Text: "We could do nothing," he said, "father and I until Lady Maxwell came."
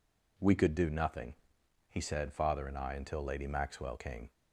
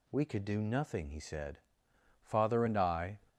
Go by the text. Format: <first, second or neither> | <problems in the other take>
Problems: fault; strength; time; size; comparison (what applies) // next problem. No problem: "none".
first | stops before "until Lady Maxwell came"; at 3.2 s